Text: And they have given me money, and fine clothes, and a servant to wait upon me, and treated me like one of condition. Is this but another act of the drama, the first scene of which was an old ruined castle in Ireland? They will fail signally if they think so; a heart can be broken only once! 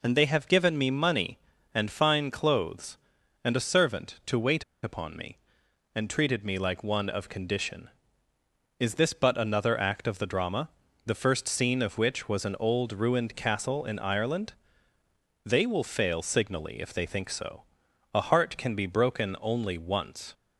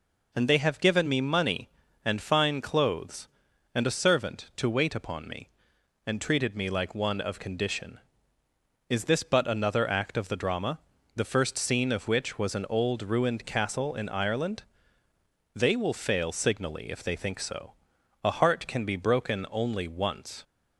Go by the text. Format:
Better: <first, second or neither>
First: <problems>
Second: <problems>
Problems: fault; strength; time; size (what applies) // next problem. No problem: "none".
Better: second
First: pauses between "wait" and "upon"; slight; at 4.6 s; 0.19 s long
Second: none